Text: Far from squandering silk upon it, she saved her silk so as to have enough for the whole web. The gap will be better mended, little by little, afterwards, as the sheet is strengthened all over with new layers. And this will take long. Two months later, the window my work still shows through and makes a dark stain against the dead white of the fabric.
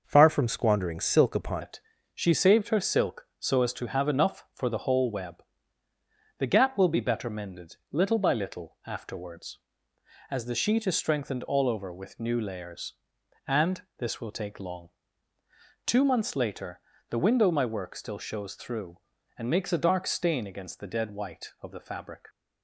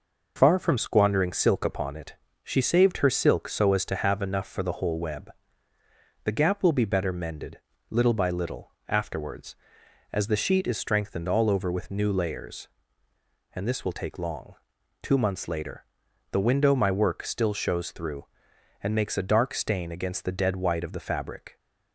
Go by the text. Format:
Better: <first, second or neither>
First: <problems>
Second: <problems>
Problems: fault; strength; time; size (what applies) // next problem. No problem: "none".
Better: second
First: changes voice at "it"; from 1.6 s on; 20.6 s long // pauses between "And" and "this"; slight; at 13.8 s; 0.16 s long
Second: none